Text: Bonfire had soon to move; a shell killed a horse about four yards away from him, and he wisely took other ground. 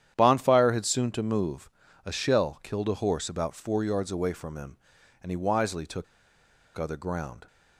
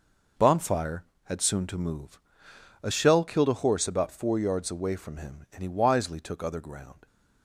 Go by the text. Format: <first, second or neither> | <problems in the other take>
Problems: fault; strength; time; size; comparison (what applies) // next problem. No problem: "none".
second | starts louder than the rest; strong; until 1.1 s; 10 dB // pauses between "took" and "other"; noticeable; at 6.0 s; 0.72 s long